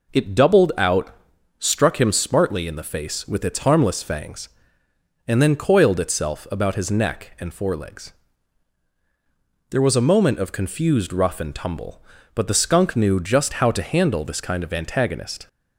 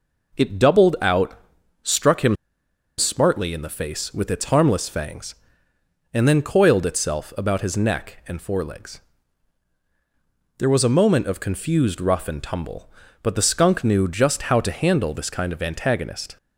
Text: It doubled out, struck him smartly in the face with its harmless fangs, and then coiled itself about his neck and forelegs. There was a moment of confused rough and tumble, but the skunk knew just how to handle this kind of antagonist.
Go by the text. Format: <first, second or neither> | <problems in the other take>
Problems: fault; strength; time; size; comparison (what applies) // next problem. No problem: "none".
first | pauses between "him" and "smartly"; noticeable; at 2.3 s; 0.63 s long